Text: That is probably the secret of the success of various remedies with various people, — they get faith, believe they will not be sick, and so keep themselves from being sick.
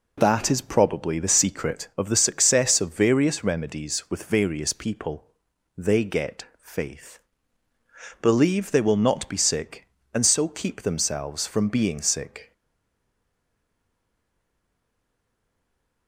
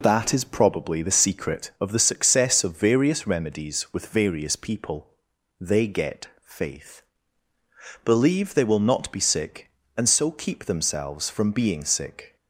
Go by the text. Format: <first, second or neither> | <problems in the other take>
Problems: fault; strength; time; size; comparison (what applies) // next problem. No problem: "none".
second | pauses between "get" and "faith"; slight; at 6.4 s; 0.18 s long; slight in the second // stays silent after the last word; strong; from 12.5 s on; 3.5 s long